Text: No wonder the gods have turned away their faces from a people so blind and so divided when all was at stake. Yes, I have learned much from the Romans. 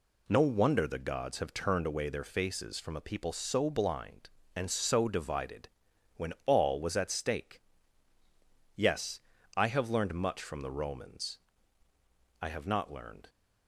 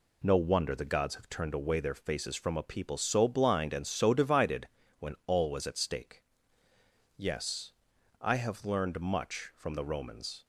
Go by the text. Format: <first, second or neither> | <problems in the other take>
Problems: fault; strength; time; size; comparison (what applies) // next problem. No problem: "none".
second | pauses between "divided" and "when"; noticeable; at 5.6 s; 0.48 s long; slight in the second // goes on to say "I have not learned"; noticeable; from 12.3 s on; 0.88 s long